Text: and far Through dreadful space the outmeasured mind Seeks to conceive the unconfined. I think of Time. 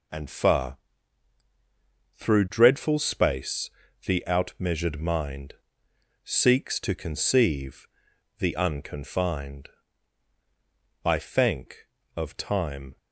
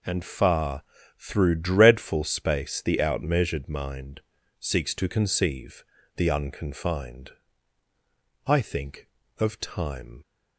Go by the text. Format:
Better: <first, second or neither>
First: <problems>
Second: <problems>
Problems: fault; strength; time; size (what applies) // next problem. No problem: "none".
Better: second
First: pauses between "far" and "Through"; strong; at 0.7 s; 1.3 s long // pauses between "space" and "the"; slight; at 3.6 s; 0.36 s long // pauses between "mind" and "Seeks"; noticeable; at 5.5 s; 0.70 s long // pauses between "conceive" and "the"; noticeable; at 7.8 s; 0.52 s long // says "thank" for "think"; at 11.1 s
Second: pauses between "far" and "Through"; slight; at 0.8 s; 0.36 s long // pauses between "mind" and "Seeks"; at 4.2 s; 0.38 s long // pauses between "conceive" and "the"; slight; at 5.8 s; 0.34 s long